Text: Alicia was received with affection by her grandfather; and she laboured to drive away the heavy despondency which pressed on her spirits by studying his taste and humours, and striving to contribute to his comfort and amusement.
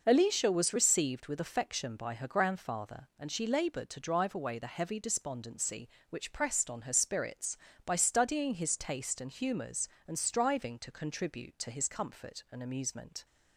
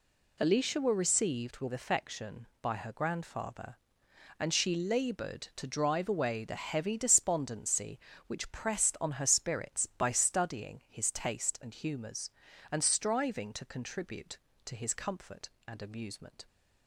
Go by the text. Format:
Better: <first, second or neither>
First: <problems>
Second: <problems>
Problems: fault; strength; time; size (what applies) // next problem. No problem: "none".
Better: first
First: none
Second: says "were" for "was"; at 0.7 s